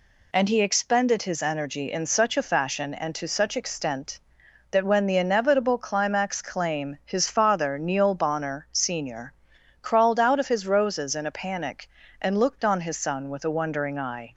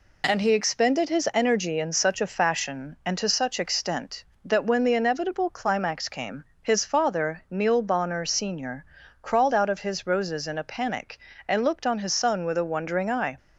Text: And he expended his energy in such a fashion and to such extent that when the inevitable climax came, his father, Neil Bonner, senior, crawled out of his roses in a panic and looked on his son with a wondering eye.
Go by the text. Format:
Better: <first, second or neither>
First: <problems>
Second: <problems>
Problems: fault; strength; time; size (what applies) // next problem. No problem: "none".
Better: second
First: says "claim" for "came"; at 6.4 s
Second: none